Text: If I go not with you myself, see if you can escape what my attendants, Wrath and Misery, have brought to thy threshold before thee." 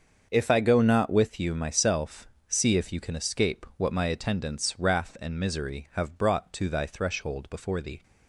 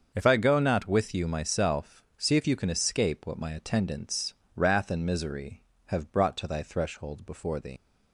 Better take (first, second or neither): first